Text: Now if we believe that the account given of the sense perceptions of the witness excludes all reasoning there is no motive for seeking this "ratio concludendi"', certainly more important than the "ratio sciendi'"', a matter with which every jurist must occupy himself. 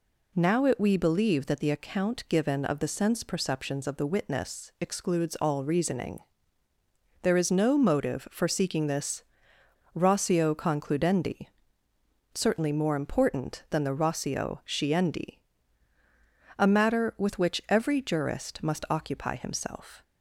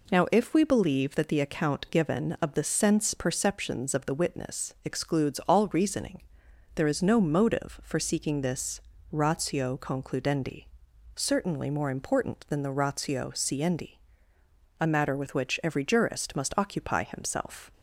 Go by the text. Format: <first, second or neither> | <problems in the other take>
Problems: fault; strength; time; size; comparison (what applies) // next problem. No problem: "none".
second | says "it" for "if"; at 0.6 s // pauses between "reasoning" and "there"; at 6.1 s; 1.0 s long; noticeable in the second // pauses between "this" and "ratio"; noticeable; at 9.2 s; 0.70 s long; slight in the second